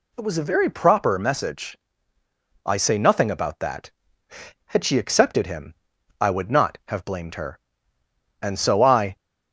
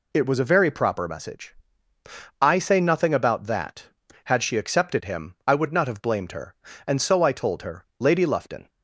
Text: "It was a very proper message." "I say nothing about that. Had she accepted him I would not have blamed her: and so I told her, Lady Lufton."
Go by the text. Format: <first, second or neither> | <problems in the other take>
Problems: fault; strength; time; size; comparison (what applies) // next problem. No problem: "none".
second | pauses between "him" and "I"; noticeable; at 5.7 s; 0.48 s long // stops before "told her Lady Lufton"; at 9.1 s